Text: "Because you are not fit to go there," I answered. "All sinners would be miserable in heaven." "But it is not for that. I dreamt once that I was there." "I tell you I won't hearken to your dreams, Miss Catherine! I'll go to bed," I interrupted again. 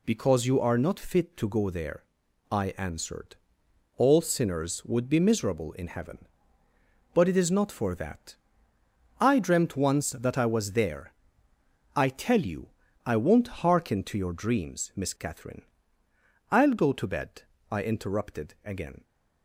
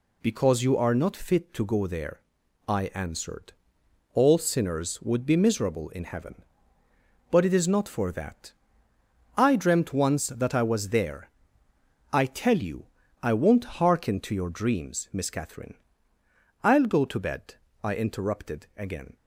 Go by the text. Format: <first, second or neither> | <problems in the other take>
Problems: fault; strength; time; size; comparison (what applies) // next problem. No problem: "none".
neither | pauses between "you" and "I"; the same in both